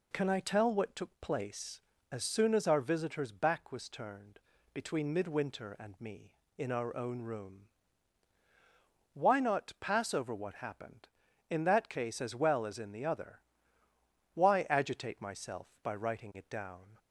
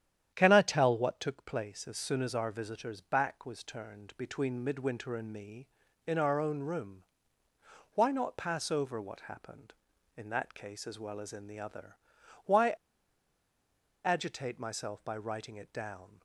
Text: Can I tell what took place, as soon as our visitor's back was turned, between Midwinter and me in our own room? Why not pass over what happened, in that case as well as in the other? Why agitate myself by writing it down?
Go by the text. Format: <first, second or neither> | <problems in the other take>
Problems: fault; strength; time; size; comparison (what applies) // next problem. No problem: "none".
first | starts louder than the rest; strong; until 1.3 s; 10 dB // pauses between "Why" and "agitate"; strong; at 12.7 s; 1.3 s long